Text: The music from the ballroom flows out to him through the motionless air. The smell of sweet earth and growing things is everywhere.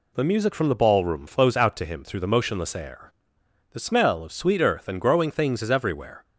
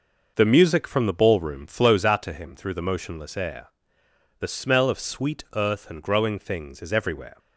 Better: first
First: none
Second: starts louder than the rest; noticeable; until 2.1 s; 6 dB

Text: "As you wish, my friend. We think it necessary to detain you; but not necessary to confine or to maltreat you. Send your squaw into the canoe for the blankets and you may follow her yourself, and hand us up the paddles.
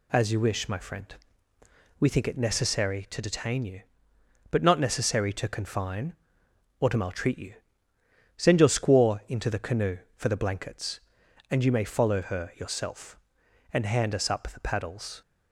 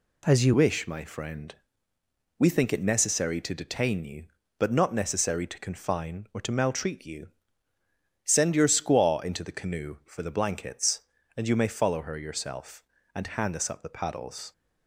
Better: first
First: none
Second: changes voice at "wish"; from 0.5 s on; 14.0 s long

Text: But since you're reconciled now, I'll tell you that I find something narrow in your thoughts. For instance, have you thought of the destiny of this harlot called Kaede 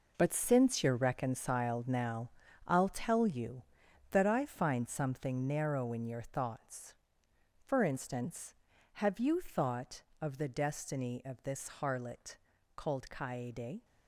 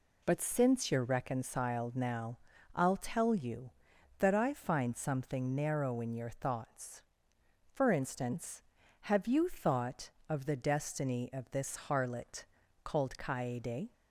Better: second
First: gets quieter; strong; throughout; 10.5 dB // pauses between "harlot" and "called"; at 12.3 s; 0.40 s long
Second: pauses between "harlot" and "called"; at 12.4 s; 0.40 s long

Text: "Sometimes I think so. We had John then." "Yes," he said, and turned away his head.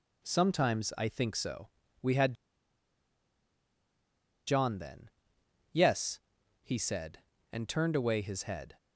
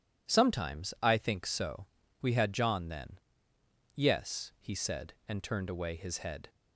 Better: second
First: pauses between "had" and "John"; strong; at 2.3 s; 2.1 s long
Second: none

